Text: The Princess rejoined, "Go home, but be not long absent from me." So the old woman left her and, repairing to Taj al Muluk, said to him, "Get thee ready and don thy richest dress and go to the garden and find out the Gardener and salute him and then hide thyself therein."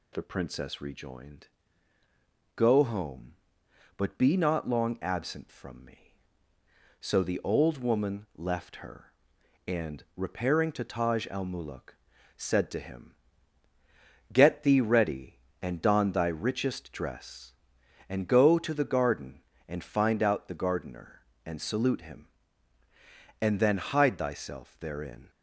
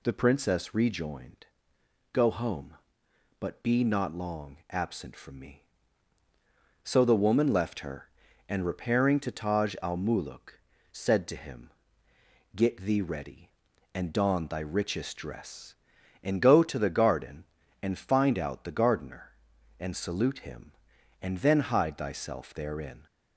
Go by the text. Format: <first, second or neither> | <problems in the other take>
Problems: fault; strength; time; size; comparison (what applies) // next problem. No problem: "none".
first | skips "old"; at 7.2 s